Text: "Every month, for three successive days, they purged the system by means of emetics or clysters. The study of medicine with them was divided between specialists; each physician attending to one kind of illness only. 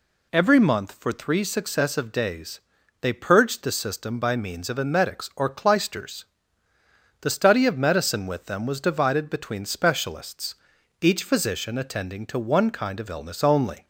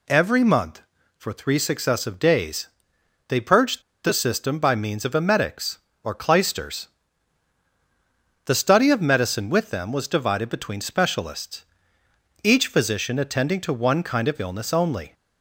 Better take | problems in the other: first | pauses between "purged" and "the"; slight; at 3.8 s; 0.22 s long

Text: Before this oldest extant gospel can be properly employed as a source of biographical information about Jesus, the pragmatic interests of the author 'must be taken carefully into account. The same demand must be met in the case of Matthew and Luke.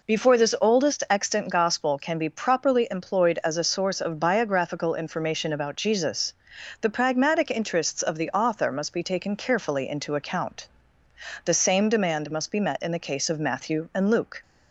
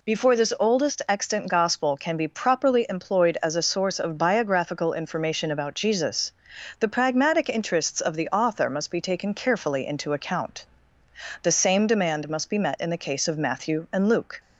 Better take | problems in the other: second | starts louder than the rest; noticeable; until 1.5 s; 4 dB

